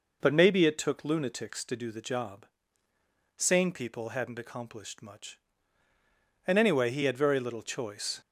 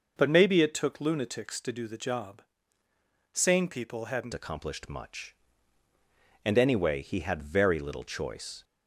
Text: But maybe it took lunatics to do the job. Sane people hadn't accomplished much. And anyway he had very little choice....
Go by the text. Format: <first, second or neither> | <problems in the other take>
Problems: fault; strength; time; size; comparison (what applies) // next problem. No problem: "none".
first | changes voice at "accomplished"; from 4.3 s on; 4.3 s long